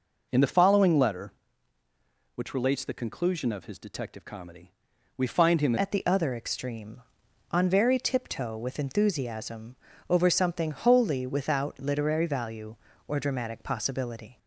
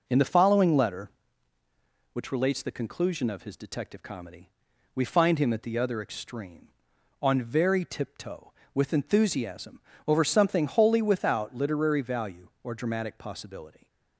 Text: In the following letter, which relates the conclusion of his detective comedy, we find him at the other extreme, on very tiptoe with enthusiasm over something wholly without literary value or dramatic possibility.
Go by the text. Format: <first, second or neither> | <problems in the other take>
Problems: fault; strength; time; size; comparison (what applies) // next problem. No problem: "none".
second | changes voice at "at"; from 5.7 s on; 8.6 s long // pauses between "enthusiasm" and "over"; slight; at 9.7 s; 0.36 s long; slight in the second